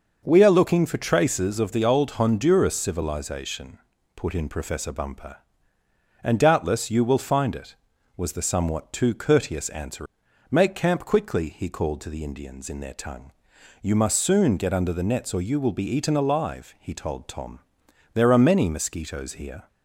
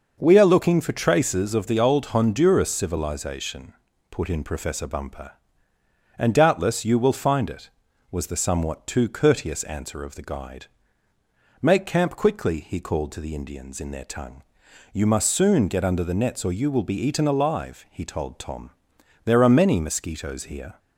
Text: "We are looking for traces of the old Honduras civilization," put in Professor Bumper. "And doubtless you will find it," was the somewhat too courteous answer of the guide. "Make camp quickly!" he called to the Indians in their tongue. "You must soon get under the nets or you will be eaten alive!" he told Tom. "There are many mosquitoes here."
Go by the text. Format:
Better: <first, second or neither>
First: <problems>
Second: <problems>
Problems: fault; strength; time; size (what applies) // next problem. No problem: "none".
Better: second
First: starts louder than the rest; until 1.2 s; 6 dB // skips "of the guide"; at 10.2 s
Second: starts louder than the rest; until 1.2 s; 6 dB